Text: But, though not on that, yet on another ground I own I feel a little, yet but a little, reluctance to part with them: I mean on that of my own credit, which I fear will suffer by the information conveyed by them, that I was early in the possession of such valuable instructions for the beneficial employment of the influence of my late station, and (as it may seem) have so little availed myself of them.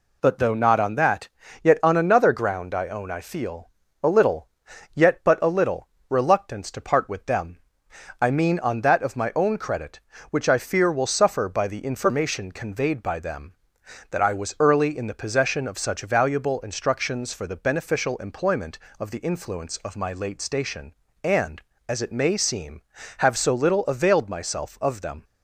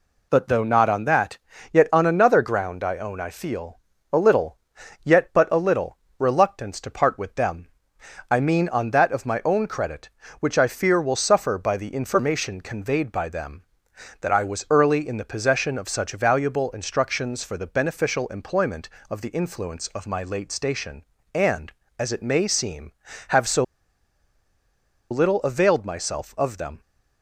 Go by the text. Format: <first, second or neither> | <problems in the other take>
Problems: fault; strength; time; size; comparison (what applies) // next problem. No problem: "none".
first | pauses between "feel" and "a"; slight; at 3.7 s; 0.34 s long; slight in the first // pauses between "so" and "little"; strong; at 23.6 s; 1.4 s long